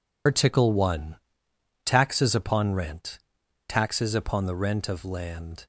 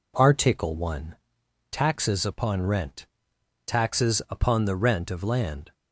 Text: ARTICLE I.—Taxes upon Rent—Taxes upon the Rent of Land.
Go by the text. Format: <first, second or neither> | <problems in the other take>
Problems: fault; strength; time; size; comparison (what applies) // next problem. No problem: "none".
second | loses the start of "ARTICLE"; at 0.2 s; 100 ms